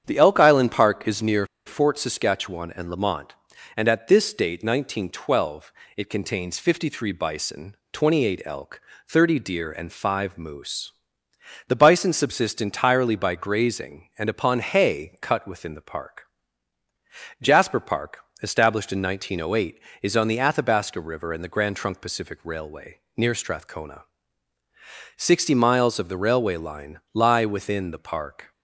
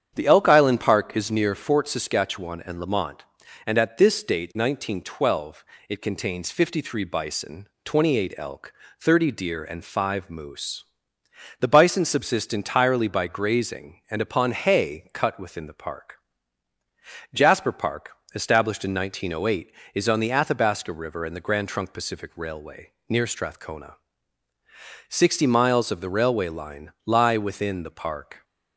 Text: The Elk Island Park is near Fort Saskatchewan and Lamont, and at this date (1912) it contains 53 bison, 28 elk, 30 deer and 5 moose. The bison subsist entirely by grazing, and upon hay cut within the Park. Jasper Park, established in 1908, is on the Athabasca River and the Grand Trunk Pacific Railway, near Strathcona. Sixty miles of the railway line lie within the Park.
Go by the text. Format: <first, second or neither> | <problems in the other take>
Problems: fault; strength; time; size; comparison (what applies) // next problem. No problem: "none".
second | starts louder than the rest; strong; until 1.0 s; 8.5 dB; strong in the second // pauses between "near" and "Fort"; slight; at 1.4 s; 0.19 s long